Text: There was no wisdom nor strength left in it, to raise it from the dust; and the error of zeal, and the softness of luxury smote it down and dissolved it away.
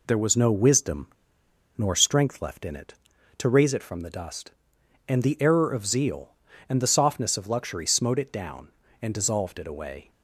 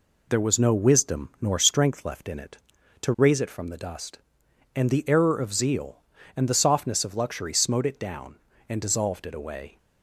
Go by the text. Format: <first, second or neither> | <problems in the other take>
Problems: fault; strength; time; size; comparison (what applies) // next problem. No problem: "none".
second | pauses between "wisdom" and "nor"; noticeable; at 1.0 s; 0.68 s long